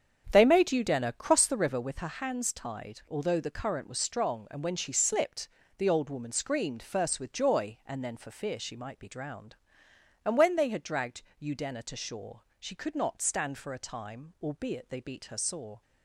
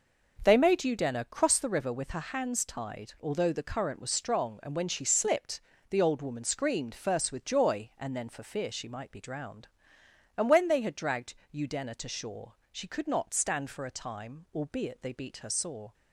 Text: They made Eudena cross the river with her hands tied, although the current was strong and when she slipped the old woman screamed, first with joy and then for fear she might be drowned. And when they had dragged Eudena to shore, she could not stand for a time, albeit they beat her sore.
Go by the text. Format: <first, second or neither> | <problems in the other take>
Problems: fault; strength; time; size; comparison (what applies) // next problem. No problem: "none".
second | starts louder than the rest; strong; until 1.9 s; 8 dB // pauses between "slipped" and "the"; slight; at 5.4 s; 0.30 s long; slight in the second // pauses between "dragged" and "Eudena"; slight; at 11.2 s; 0.18 s long; slight in the second